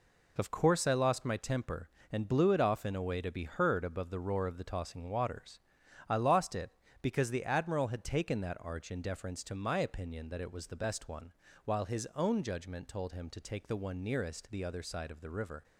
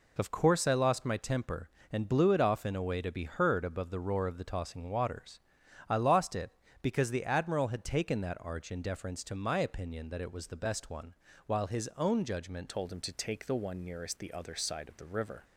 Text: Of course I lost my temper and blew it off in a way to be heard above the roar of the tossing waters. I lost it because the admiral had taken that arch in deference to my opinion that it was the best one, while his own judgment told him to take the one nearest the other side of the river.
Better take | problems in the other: first | changes voice at "told"; from 12.6 s on; 2.8 s long

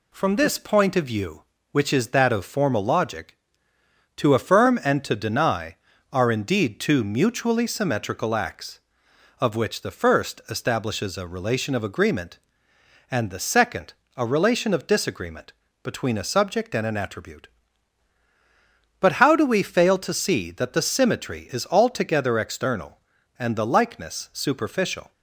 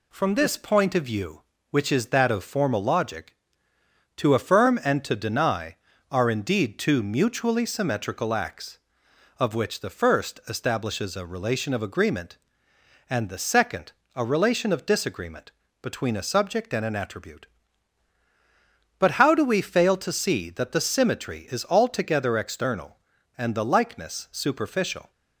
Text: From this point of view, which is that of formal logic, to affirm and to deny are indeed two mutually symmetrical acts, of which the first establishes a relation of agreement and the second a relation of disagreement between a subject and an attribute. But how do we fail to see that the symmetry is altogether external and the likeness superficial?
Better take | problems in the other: neither | pauses between "second" and "a"; slight; the same in both // pauses between "disagreement" and "between"; slight; the same in both

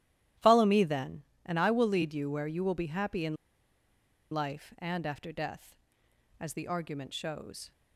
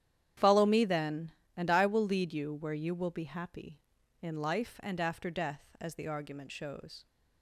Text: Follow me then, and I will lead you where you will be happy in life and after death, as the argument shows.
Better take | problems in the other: second | starts louder than the rest; strong; until 1.6 s; 12.5 dB; strong in the second // pauses between "in" and "life"; noticeable; at 3.3 s; 0.97 s long

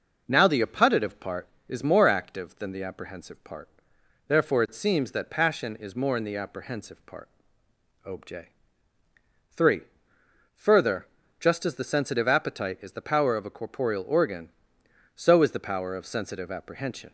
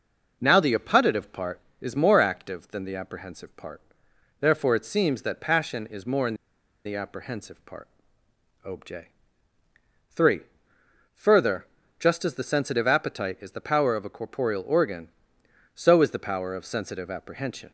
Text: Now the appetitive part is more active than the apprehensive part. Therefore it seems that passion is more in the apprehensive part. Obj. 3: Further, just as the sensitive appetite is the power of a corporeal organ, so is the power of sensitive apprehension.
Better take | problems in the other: first | pauses between "in" and "the"; noticeable; at 6.3 s; 0.49 s long

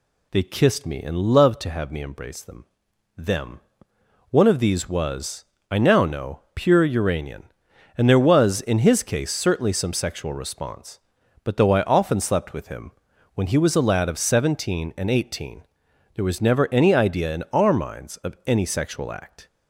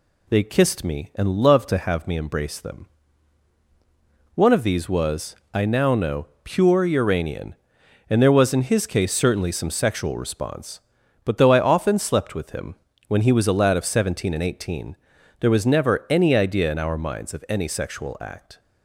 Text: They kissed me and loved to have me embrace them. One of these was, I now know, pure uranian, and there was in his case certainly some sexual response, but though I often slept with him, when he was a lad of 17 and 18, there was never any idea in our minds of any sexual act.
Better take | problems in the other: second | says "them" twice; at 3.1 s

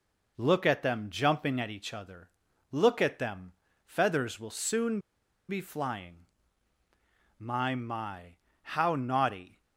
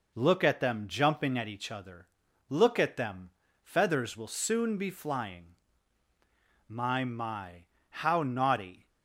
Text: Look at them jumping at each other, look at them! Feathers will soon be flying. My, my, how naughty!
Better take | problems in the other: second | pauses between "soon" and "be"; noticeable; at 4.9 s; 0.49 s long

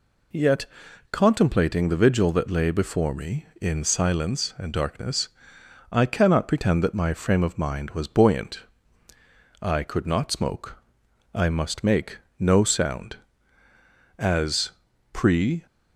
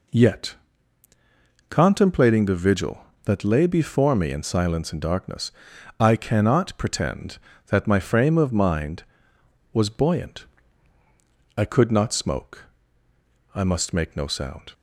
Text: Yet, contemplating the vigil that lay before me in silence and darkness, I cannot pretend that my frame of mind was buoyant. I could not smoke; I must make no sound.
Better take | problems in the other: second | pauses between "make" and "no"; slight; at 12.1 s; 0.20 s long // goes on to say "As pre"; from 14.1 s on; 1.4 s long

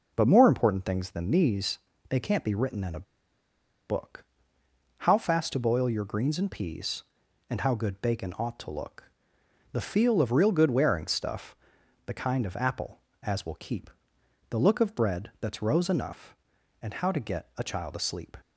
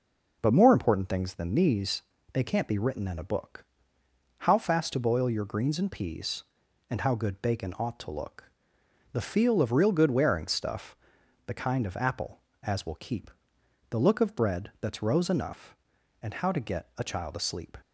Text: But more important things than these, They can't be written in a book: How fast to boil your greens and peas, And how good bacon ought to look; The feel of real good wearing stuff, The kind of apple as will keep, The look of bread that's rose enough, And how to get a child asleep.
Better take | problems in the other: second | pauses between "a" and "book"; noticeable; at 3.0 s; 0.83 s long

